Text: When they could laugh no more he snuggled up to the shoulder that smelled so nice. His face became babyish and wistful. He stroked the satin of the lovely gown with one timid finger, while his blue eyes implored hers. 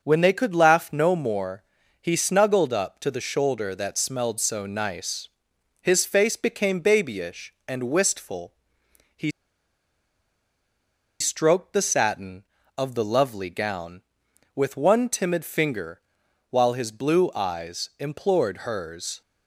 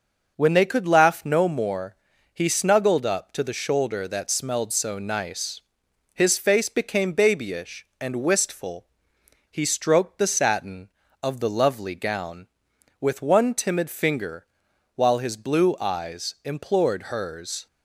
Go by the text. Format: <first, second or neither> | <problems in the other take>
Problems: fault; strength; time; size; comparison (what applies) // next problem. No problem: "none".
second | starts louder than the rest; noticeable; until 1.0 s; 6 dB; noticeable in the second // pauses between "more" and "he"; at 1.6 s; 0.40 s long; also in the second // pauses between "He" and "stroked"; strong; at 9.2 s; 1.9 s long